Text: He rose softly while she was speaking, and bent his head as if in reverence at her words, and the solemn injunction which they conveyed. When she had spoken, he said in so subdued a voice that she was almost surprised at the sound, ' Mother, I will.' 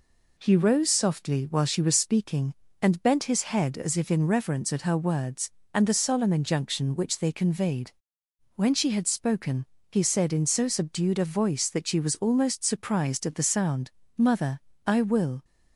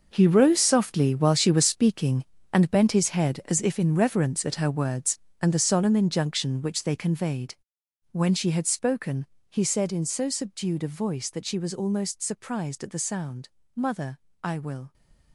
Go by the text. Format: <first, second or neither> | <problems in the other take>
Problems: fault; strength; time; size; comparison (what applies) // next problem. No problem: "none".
first | gets quieter; strong; throughout; 15 dB